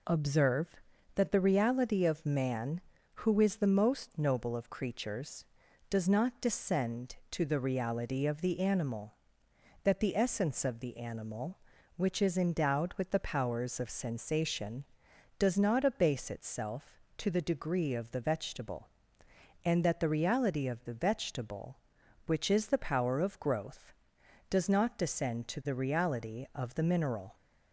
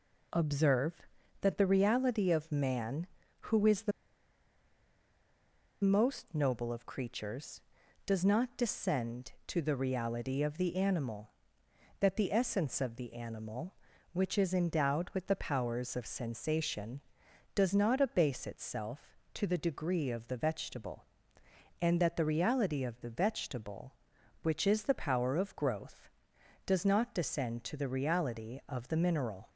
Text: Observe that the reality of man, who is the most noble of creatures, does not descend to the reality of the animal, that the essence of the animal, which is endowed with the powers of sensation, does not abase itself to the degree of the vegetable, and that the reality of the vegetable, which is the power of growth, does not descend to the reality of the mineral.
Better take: first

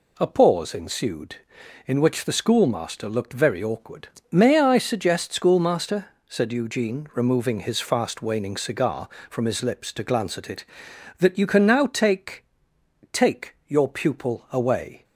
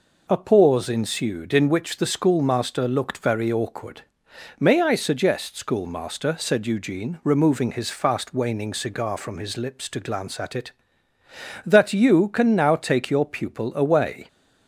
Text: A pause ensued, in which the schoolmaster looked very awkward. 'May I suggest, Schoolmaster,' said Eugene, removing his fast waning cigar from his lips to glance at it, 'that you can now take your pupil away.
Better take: second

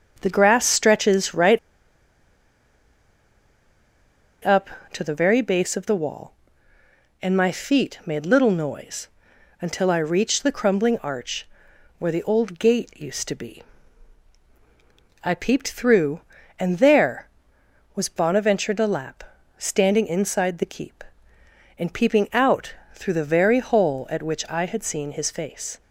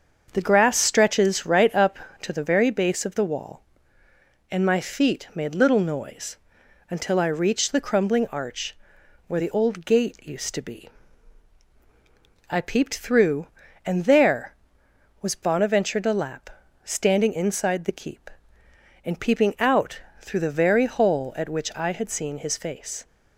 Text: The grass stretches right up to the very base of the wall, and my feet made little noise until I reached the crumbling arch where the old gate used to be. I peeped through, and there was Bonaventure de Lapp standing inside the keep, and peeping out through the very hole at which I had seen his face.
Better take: second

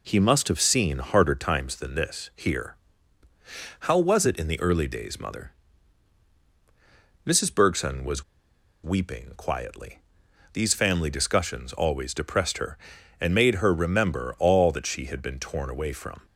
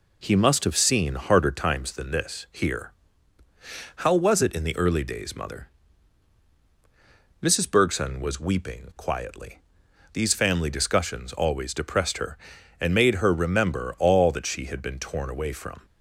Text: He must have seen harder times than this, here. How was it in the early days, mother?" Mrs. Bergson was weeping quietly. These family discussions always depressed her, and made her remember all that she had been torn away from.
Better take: second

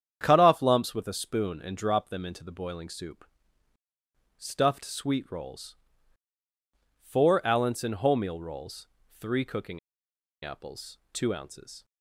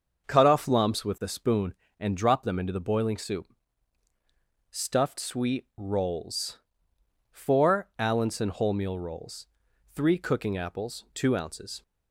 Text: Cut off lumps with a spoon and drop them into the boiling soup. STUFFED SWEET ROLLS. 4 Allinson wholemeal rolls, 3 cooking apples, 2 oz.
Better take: second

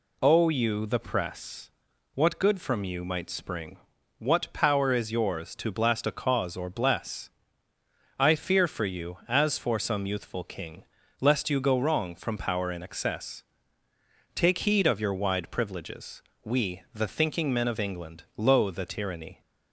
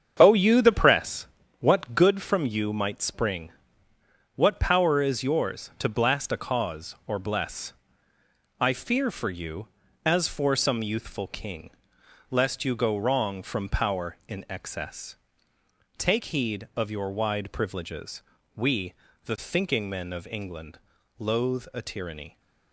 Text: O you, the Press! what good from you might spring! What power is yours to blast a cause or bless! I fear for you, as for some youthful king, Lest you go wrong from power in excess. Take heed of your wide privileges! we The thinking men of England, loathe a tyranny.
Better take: first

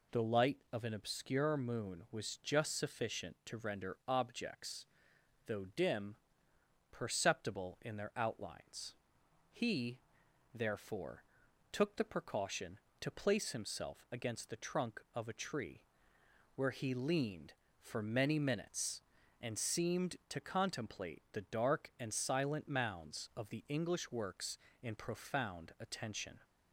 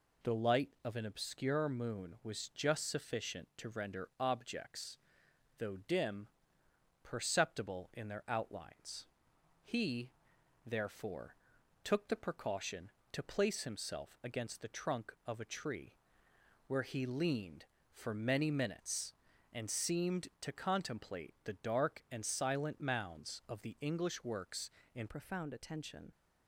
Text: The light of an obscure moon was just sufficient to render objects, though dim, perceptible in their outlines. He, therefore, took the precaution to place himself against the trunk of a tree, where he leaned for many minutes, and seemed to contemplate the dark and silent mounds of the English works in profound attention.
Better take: first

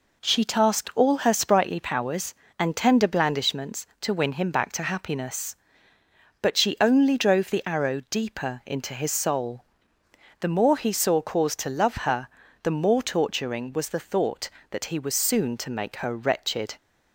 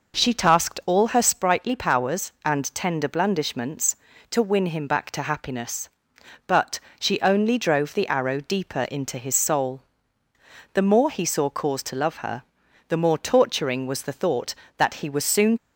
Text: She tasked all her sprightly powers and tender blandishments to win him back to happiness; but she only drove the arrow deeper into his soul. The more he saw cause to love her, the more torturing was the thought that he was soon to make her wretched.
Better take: first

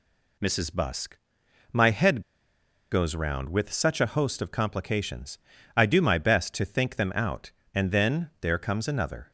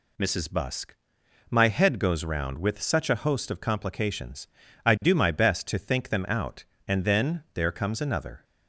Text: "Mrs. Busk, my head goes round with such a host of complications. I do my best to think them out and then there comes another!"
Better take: second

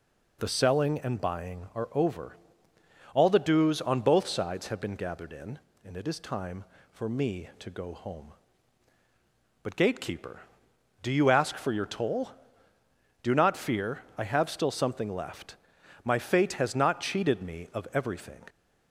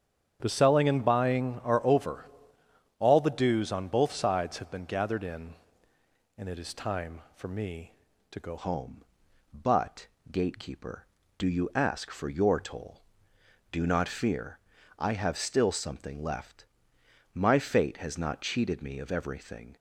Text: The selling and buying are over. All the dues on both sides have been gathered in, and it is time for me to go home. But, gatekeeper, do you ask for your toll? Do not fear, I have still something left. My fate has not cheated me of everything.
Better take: first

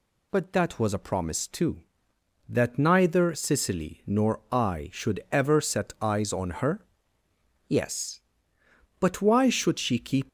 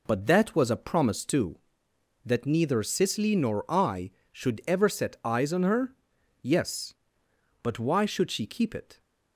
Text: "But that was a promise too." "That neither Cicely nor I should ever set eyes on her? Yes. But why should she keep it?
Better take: second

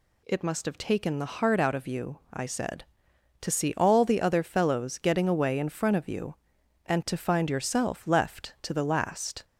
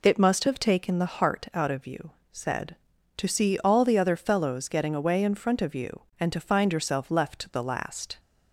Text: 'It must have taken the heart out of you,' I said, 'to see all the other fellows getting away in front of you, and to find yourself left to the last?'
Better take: first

